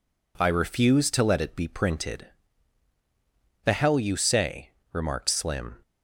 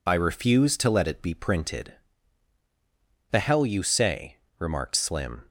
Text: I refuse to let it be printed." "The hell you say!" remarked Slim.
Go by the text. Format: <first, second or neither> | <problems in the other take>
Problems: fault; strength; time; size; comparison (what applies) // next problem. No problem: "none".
first | loses the start of "I"; at 0.0 s; 45 ms